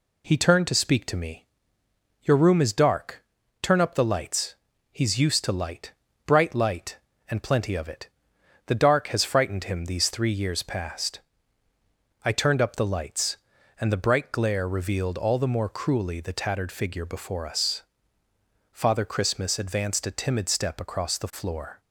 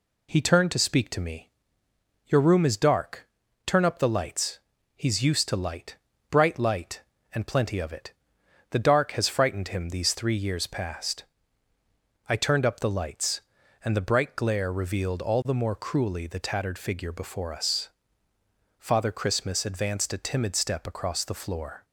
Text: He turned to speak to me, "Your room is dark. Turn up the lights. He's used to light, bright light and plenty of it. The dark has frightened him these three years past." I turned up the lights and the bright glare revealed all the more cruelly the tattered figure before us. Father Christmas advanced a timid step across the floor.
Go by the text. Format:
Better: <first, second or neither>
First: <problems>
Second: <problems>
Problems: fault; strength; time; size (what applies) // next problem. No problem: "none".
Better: neither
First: none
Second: none